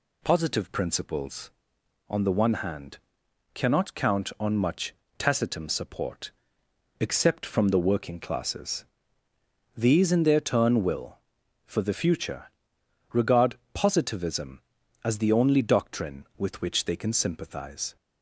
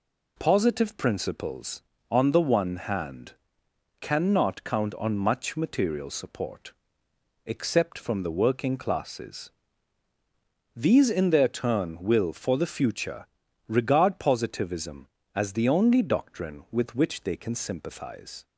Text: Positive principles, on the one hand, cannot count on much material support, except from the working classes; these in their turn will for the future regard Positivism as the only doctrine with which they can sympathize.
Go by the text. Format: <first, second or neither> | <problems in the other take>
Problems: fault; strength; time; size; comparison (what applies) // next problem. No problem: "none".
second | says "tacitum" for "material"; at 5.1 s // pauses between "future" and "regard"; noticeable; at 12.5 s; 0.60 s long; also in the second // pauses between "regard" and "Positivism"; slight; at 13.5 s; 0.18 s long